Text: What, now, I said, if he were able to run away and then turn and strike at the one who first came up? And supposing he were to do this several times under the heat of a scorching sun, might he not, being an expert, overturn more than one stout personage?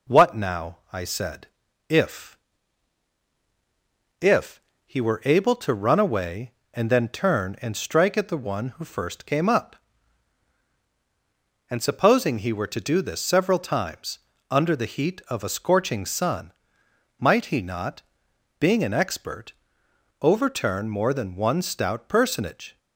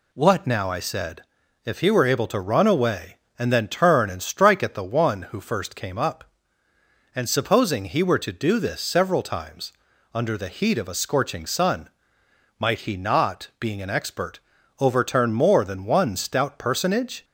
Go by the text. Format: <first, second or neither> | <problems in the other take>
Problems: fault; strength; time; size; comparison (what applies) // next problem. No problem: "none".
second | says "if" twice; at 4.1 s // pauses between "times" and "under"; slight; at 14.1 s; 0.32 s long; also in the second